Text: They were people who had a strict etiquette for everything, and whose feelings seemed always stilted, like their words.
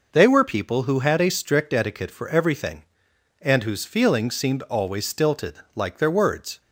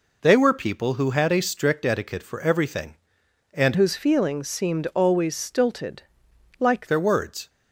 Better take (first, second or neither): first